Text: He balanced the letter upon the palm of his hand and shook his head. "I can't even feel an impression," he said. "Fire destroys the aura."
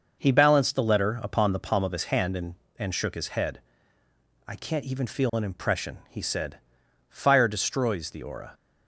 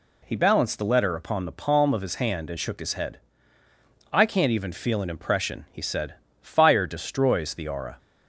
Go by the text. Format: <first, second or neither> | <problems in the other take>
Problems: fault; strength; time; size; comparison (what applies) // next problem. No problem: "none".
second | says "and" twice; at 2.8 s